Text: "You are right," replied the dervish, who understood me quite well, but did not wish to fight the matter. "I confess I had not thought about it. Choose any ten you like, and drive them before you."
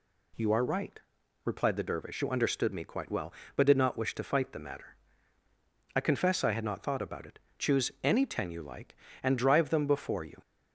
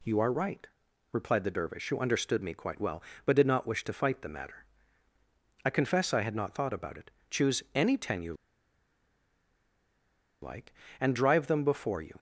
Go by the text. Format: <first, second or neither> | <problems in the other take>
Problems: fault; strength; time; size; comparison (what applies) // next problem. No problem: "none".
first | pauses between "you" and "like"; strong; at 8.3 s; 2.0 s long